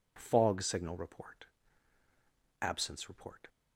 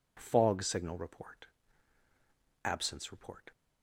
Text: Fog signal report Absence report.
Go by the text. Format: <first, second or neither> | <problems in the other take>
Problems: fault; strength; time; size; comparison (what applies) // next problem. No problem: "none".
neither | pauses between "report" and "Absence"; the same in both